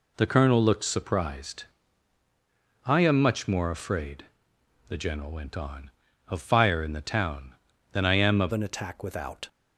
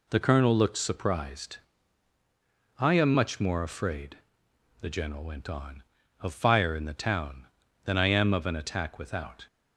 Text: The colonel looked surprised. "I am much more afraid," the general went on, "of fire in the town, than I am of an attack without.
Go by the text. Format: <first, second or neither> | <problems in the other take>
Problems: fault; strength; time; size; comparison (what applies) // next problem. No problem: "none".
second | changes voice at "an"; from 8.5 s on; 0.9 s long